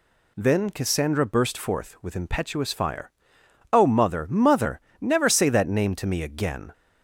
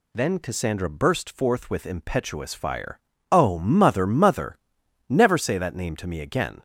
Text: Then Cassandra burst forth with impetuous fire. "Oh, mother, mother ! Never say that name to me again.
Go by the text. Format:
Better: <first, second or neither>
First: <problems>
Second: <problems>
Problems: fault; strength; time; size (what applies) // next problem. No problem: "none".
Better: neither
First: none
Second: none